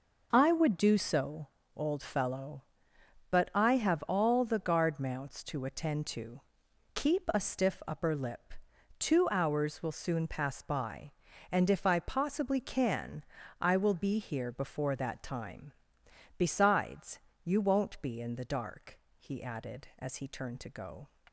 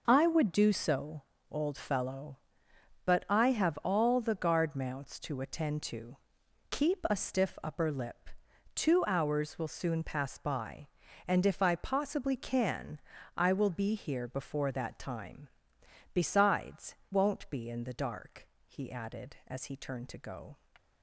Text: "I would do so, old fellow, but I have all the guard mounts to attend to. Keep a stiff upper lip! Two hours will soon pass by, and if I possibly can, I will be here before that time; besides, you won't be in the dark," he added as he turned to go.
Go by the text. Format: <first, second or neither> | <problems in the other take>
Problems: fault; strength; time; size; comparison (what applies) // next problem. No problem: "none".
first | skips "you"; at 17.0 s